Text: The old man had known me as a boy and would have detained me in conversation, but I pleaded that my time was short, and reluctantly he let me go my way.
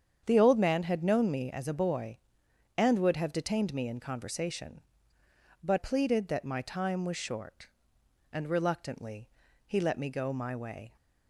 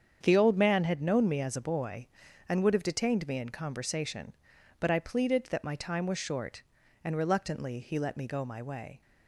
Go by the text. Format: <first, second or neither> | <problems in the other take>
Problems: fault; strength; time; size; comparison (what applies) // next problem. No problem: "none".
second | starts louder than the rest; strong; until 1.2 s; 8 dB; strong in the second // skips "I"; at 5.7 s // pauses between "reluctantly" and "he"; slight; at 9.2 s; 0.36 s long